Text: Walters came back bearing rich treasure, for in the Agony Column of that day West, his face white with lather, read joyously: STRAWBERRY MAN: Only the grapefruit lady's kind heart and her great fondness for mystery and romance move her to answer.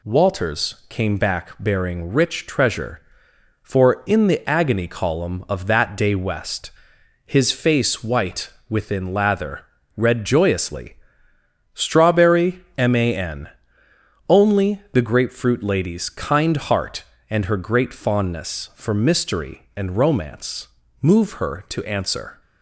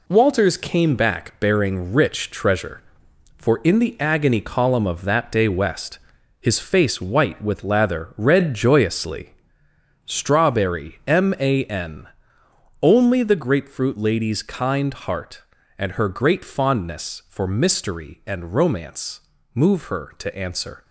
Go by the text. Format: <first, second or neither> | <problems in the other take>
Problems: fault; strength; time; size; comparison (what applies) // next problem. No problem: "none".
second | says "within" for "with"; at 8.6 s // pauses between "romance" and "move"; slight; at 20.6 s; 0.34 s long; slight in the second